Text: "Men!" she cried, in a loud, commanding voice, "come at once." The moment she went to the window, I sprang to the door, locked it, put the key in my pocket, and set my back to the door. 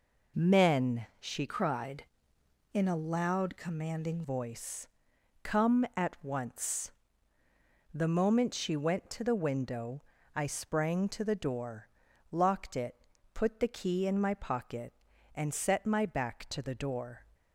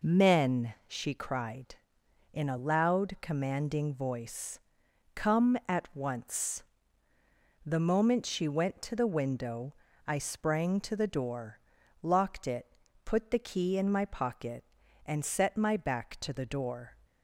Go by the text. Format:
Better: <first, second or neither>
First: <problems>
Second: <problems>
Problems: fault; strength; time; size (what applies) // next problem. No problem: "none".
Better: second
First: changes voice from "cried" to "commanding"; from 1.4 to 4.2 s; 2.8 s long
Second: none